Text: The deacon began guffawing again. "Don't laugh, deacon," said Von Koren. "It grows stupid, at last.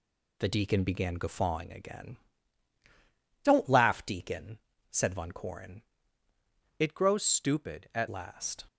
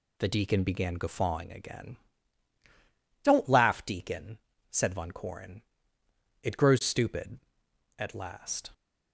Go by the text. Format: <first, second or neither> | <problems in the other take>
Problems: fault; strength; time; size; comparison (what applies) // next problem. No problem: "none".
second | changes voice from "It" to "at"; from 6.7 to 8.0 s; 1.3 s long